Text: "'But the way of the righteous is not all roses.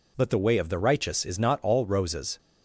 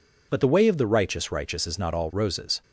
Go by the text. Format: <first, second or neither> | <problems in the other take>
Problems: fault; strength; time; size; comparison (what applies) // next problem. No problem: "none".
first | says "righteous" twice; at 1.3 s